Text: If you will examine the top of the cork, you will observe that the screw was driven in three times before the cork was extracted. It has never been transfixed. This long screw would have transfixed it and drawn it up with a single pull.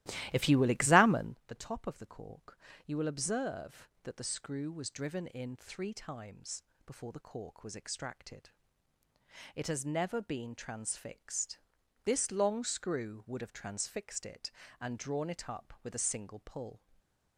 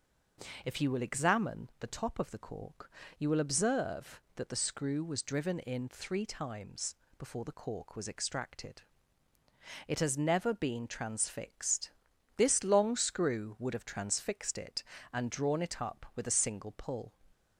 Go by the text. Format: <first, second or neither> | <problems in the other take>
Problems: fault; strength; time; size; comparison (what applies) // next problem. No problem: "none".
second | starts louder than the rest; strong; until 1.4 s; 15.5 dB // pauses between "times" and "before"; slight; at 6.6 s; 0.22 s long; slight in the second // stays silent after the last word; slight; from 16.7 s on; 0.6 s long